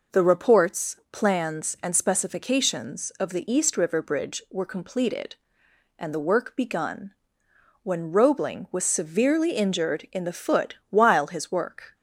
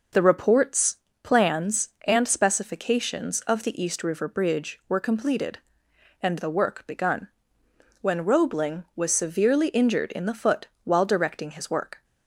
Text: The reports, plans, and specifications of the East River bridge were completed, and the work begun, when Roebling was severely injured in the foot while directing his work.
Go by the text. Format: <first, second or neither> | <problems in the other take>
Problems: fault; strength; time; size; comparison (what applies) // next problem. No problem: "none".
second | pauses between "foot" and "while"; slight; at 10.7 s; 0.16 s long; slight in the second // skips "directing"; at 11.2 s